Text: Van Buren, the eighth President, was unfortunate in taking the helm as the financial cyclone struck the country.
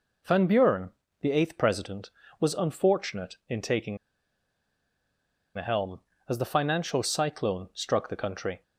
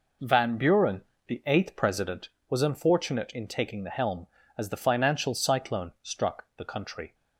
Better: second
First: pauses between "taking" and "the"; strong; at 3.9 s; 1.5 s long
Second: none

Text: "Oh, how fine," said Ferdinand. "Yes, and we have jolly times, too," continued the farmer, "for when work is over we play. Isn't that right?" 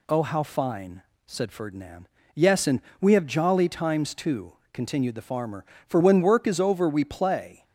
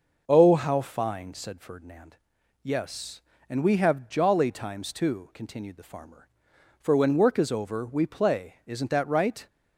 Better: second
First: pauses between "and" and "we"; slight; at 2.8 s; 0.18 s long // stops before "Isn't that right"; at 7.6 s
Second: none

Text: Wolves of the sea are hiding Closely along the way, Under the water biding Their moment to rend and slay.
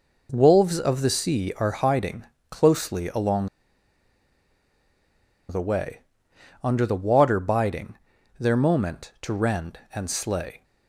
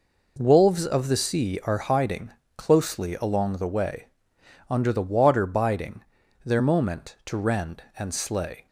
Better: second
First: pauses between "hiding" and "Closely"; slight; at 2.2 s; 0.28 s long // pauses between "along" and "the"; strong; at 3.4 s; 2.0 s long // pauses between "biding" and "Their"; at 7.9 s; 0.42 s long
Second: pauses between "hiding" and "Closely"; slight; at 2.2 s; 0.28 s long // pauses between "biding" and "Their"; at 6.0 s; 0.41 s long

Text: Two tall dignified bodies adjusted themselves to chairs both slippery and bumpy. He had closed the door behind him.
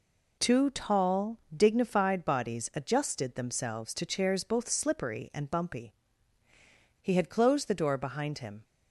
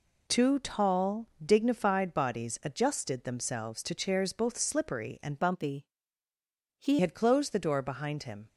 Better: first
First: pauses between "tall" and "dignified"; slight; at 1.3 s; 0.18 s long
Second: pauses between "tall" and "dignified"; slight; at 1.2 s; 0.18 s long // changes voice from "bumpy" to "He"; from 5.3 to 6.9 s; 1.6 s long

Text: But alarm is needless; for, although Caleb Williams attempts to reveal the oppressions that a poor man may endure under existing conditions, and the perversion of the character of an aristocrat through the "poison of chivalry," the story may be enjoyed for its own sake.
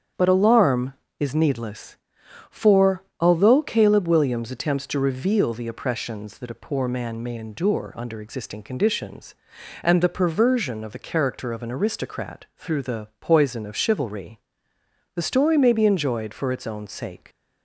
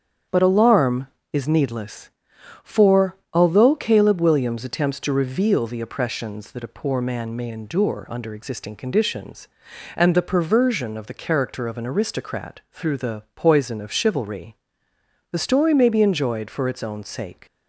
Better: neither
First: starts louder than the rest; strong; until 1.4 s; 8 dB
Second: starts louder than the rest; strong; until 1.5 s; 8 dB

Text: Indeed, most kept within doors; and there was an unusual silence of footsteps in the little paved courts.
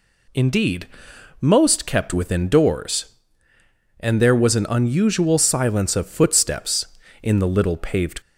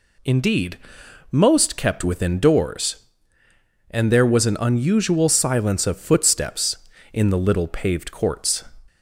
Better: second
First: stops before "courts"; at 8.2 s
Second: none

